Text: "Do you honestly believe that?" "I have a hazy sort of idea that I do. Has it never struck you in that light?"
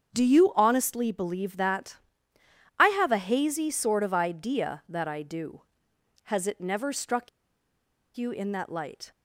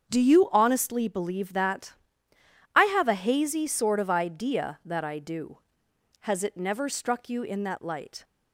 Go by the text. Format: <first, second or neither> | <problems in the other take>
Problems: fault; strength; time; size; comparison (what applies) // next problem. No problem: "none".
second | starts louder than the rest; strong; until 1.1 s; 7.5 dB; strong in the second // pauses between "struck" and "you"; noticeable; at 7.2 s; 0.87 s long